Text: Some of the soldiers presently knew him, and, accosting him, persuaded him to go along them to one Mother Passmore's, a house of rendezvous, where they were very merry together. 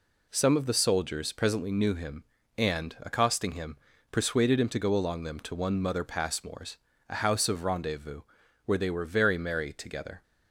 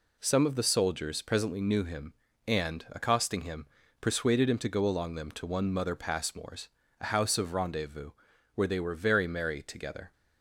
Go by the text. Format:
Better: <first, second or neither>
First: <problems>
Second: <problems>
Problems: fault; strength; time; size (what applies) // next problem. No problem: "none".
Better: neither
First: none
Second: none